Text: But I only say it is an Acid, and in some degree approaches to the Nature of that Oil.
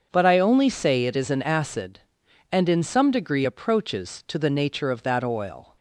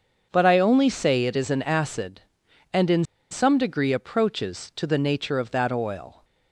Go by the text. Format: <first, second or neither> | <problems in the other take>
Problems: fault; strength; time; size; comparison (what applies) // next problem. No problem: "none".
first | starts louder than the rest; until 1.3 s; 6.5 dB; also in the first // pauses between "in" and "some"; slight; at 3.0 s; 0.28 s long